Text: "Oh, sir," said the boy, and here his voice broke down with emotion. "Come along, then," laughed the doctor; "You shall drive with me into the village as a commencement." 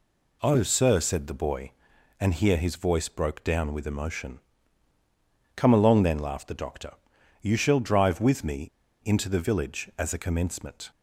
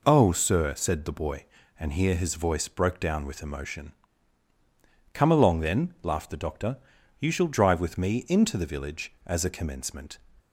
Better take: second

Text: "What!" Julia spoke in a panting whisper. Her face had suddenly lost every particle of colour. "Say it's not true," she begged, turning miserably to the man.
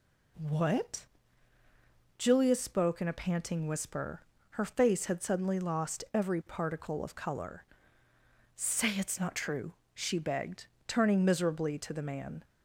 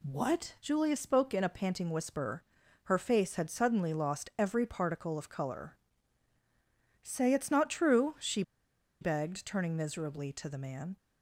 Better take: first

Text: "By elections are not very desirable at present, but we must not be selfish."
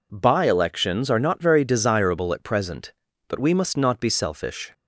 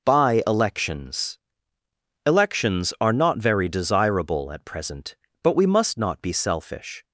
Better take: first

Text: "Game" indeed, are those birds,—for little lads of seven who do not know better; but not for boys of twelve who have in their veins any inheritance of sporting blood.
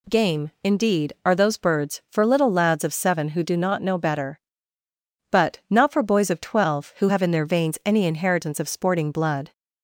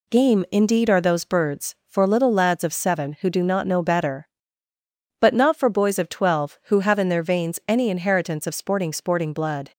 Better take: first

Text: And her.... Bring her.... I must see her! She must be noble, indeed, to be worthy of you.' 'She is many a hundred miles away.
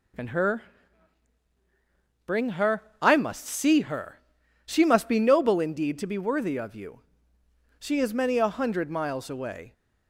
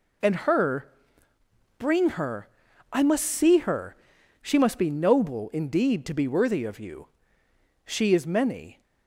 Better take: first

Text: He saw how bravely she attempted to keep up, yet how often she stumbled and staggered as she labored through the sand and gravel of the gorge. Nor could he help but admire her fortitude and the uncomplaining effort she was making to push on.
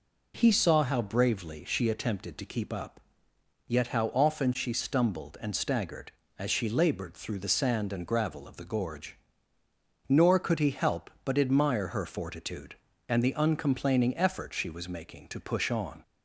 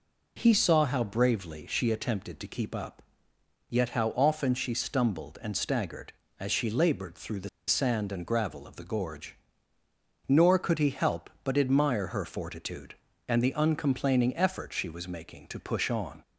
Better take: first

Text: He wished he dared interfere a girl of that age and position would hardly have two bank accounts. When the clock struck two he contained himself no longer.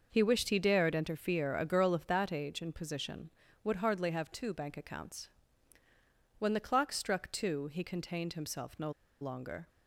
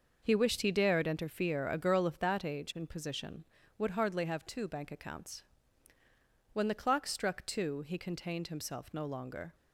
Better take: second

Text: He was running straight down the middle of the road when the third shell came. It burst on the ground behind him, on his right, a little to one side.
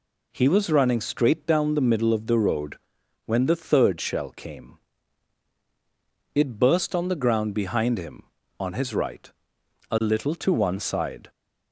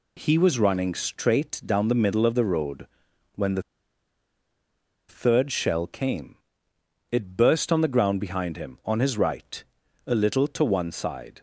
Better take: first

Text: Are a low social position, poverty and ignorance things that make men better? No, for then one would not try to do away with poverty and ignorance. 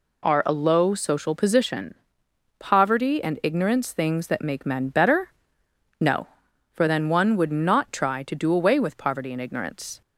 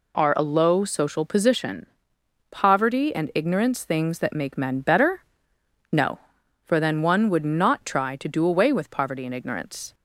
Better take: neither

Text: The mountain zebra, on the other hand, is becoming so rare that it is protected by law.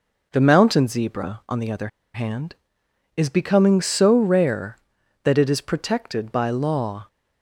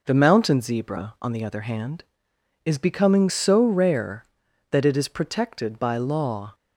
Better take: second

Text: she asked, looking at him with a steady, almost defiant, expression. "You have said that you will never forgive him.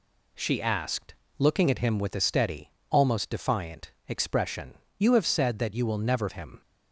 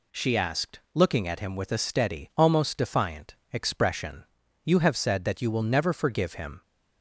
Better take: second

